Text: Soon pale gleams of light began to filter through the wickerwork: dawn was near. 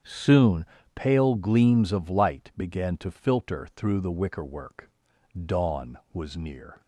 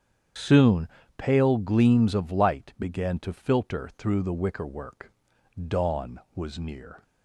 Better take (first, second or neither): first